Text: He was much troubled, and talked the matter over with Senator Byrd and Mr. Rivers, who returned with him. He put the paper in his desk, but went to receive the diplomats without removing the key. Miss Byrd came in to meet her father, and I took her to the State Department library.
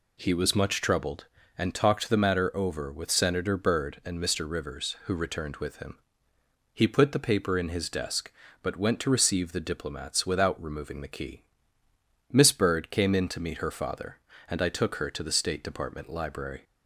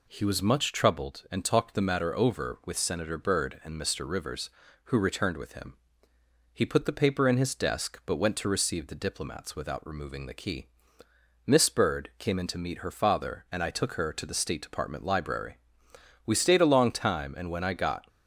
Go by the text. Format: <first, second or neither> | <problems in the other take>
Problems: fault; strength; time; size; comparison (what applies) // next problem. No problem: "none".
first | goes on to say "We stayed a long time and when I got"; strong; from 16.2 s on; 1.8 s long